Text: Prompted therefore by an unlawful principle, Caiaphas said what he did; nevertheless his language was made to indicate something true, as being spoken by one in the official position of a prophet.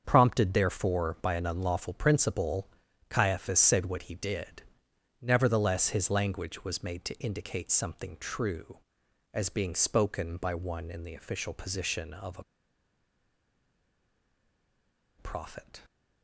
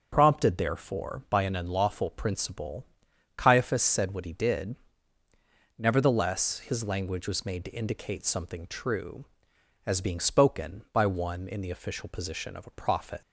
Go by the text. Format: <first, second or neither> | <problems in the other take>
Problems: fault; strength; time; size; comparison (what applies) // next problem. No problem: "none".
second | starts louder than the rest; until 1.0 s; 7 dB; also in the second // pauses between "a" and "prophet"; strong; at 12.4 s; 2.7 s long